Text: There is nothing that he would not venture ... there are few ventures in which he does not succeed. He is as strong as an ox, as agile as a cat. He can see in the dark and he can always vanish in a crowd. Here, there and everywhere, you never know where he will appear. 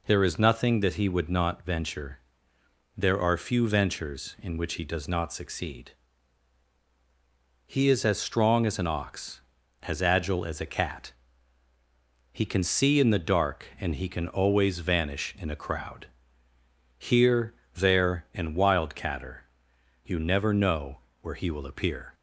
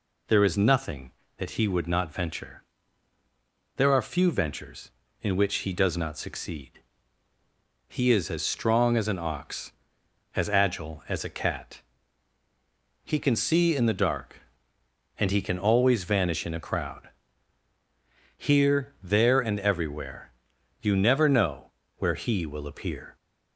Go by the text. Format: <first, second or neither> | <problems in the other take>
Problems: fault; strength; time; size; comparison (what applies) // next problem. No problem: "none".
second | says "wildcatter" for "everywhere"; at 18.5 s // pauses between "know" and "where"; slight; at 20.9 s; 0.24 s long; slight in the second